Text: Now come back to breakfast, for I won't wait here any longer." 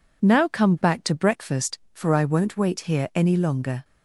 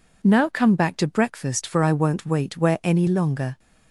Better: first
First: none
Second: says "where" for "here"; at 2.5 s

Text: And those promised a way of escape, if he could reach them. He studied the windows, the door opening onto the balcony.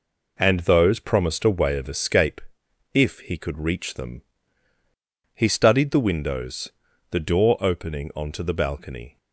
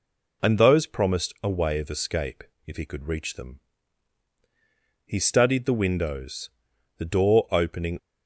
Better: first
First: none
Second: stops before "onto the balcony"; at 7.9 s

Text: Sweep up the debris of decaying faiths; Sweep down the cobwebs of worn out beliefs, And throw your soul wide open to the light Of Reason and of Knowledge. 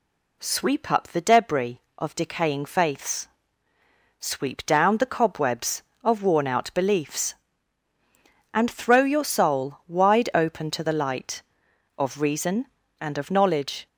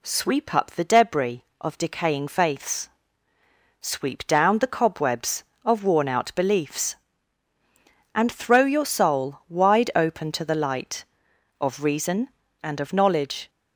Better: neither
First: none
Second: none

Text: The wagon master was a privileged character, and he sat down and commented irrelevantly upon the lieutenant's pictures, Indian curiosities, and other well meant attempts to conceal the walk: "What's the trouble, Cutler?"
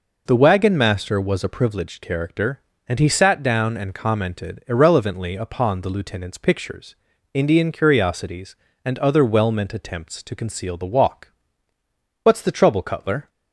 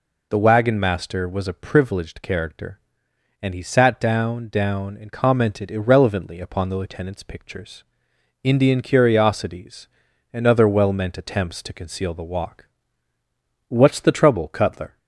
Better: first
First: none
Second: says "down" twice; at 4.4 s

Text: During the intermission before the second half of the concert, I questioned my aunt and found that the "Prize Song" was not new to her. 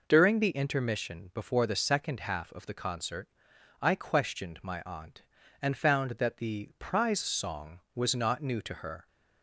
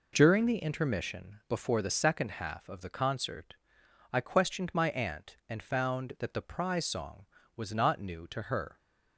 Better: neither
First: none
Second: none

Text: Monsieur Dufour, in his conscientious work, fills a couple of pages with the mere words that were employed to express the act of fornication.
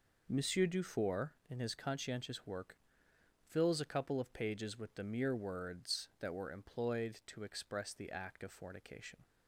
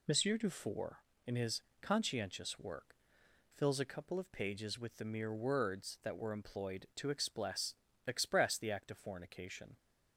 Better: first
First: none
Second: pauses between "his" and "conscientious"; slight; at 1.6 s; 0.18 s long // says "express" twice; at 8.0 s

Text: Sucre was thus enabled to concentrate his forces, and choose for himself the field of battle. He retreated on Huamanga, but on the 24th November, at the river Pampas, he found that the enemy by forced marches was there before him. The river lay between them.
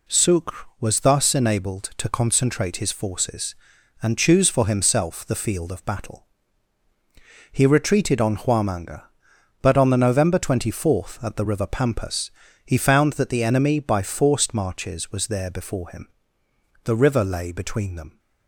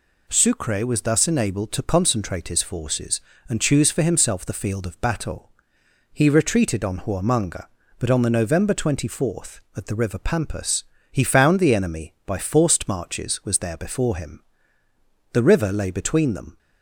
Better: first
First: none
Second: skips "that"; at 11.5 s

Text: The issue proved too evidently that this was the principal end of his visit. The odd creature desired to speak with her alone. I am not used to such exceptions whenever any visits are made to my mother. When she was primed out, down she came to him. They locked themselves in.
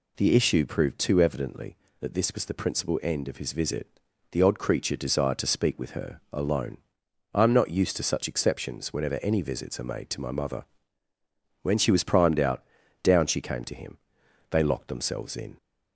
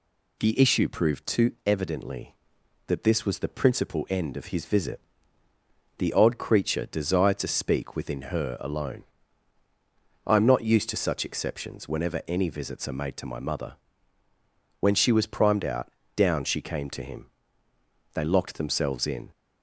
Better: first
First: none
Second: says "within" for "with"; at 7.9 s

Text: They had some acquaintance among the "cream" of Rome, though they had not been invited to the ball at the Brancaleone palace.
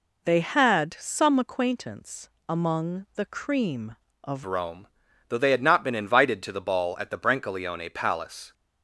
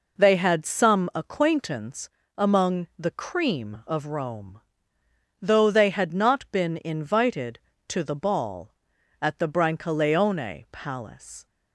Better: second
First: pauses between "acquaintance" and "among"; slight; at 2.2 s; 0.20 s long // changes voice at "Rome"; from 4.4 s on; 4.1 s long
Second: pauses between "acquaintance" and "among"; slight; at 2.0 s; 0.30 s long

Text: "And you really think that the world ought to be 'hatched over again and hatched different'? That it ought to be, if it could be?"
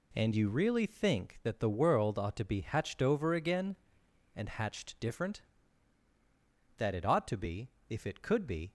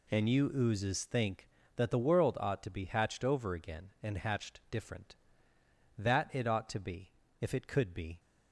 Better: first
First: none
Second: says "oozes" for "really"; at 0.5 s

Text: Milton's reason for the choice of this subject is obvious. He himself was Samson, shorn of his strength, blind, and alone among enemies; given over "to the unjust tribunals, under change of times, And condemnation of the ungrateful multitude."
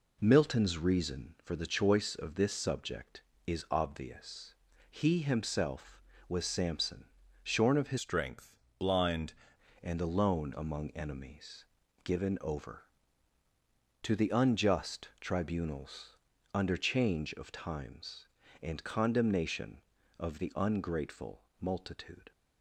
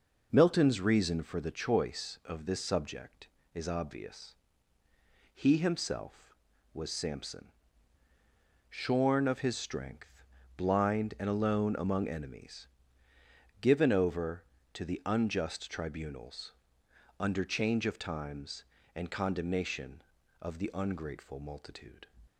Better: second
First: changes voice from "strength" to "blind"; from 7.9 to 9.3 s; 1.4 s long // pauses between "ungrateful" and "multitude"; slight; at 21.4 s; 0.18 s long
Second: none

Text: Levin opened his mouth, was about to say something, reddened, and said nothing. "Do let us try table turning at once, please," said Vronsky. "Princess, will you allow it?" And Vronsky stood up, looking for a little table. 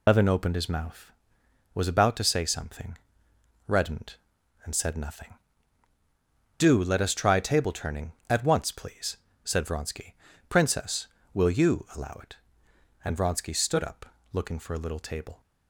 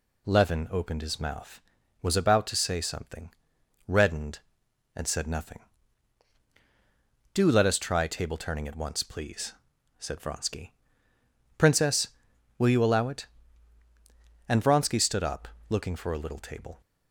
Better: second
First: loses the start of "Levin"; at 0.0 s; 120 ms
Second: none

